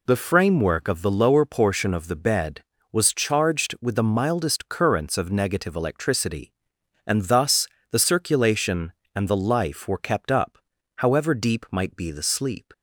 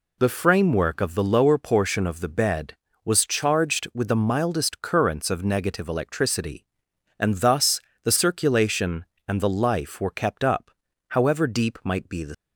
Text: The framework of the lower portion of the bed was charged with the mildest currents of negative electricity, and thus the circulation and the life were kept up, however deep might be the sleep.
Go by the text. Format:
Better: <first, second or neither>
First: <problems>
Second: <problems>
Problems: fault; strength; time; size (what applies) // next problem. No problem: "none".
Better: first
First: pauses between "thus" and "the"; slight; at 7.6 s; 0.22 s long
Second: pauses between "thus" and "the"; slight; at 7.8 s; 0.22 s long // stops before "sleep"; at 12.3 s